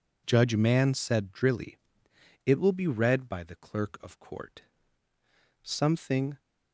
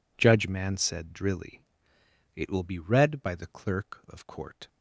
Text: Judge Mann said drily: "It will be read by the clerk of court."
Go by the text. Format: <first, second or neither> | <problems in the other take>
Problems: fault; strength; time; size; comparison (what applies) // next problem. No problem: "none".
second | goes on to say "Something"; noticeable; from 5.6 s on; 0.78 s long